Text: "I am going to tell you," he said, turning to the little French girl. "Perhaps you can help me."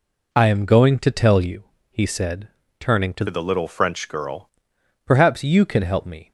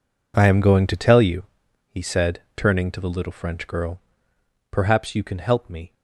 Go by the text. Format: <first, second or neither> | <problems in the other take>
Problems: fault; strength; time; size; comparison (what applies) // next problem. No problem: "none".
second | changes voice from "the" to "girl"; from 3.2 to 4.4 s; 1.2 s long